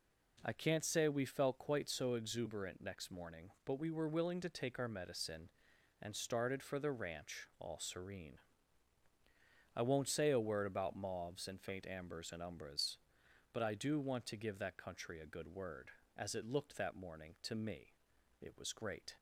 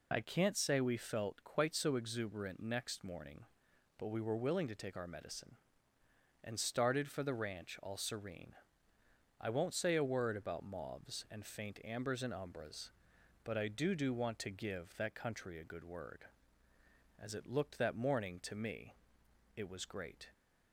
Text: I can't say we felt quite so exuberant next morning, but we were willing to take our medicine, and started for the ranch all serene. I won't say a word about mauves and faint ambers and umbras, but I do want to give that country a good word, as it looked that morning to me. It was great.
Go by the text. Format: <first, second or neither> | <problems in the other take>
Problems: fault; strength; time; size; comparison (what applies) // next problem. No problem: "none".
first | says "do" twice; at 13.9 s